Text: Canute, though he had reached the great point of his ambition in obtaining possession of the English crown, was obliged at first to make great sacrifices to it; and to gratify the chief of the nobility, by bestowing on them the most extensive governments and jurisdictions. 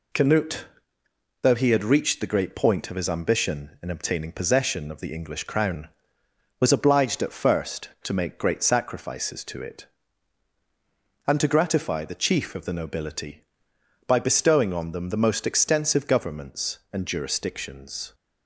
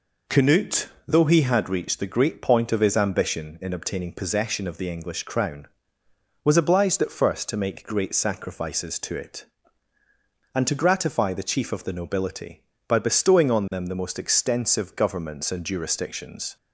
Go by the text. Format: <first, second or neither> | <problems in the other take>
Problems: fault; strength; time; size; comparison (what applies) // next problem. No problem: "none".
neither | none